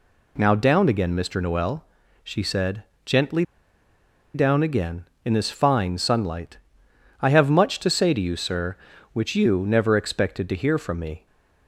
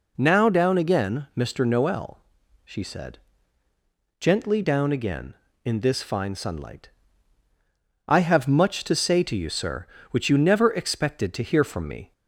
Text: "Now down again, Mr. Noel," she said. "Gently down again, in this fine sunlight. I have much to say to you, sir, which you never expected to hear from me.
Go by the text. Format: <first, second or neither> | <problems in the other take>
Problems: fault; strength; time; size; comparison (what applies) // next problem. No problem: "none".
second | pauses between "Gently" and "down"; noticeable; at 3.4 s; 0.91 s long